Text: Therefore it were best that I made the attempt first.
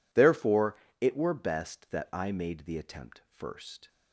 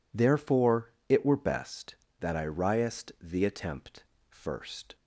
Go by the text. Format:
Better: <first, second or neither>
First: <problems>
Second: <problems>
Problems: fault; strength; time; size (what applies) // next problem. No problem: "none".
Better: first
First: pauses between "Therefore" and "it"; slight; at 0.7 s; 0.24 s long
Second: pauses between "Therefore" and "it"; slight; at 0.9 s; 0.16 s long // says "riest" for "made"; at 2.4 s // pauses between "attempt" and "first"; slight; at 4.0 s; 0.26 s long